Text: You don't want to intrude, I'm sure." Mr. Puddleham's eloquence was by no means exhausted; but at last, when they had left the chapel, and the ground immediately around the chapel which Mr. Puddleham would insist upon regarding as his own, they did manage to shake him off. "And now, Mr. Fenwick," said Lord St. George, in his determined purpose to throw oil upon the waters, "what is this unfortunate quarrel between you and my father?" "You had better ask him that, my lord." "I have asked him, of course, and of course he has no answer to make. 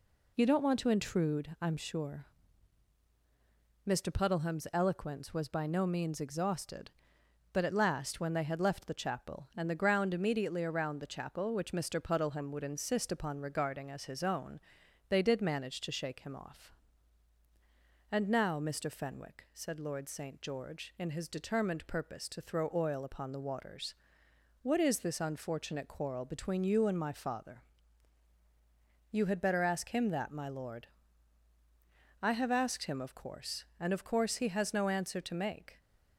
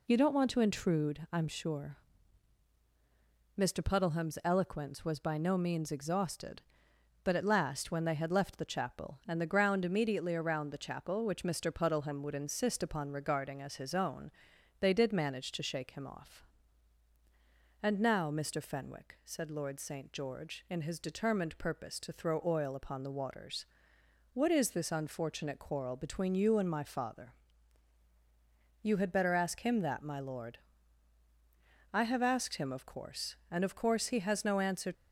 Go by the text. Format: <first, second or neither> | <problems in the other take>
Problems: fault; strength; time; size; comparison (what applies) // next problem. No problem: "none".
first | stops before "to make"; at 34.9 s